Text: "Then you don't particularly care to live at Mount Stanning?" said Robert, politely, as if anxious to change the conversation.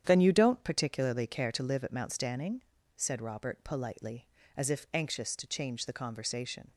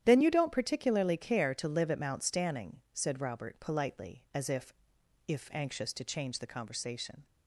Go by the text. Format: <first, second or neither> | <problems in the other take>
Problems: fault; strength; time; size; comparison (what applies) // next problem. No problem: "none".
first | starts louder than the rest; strong; until 1.0 s; 10.5 dB; strong in the first // says "if" twice; at 5.2 s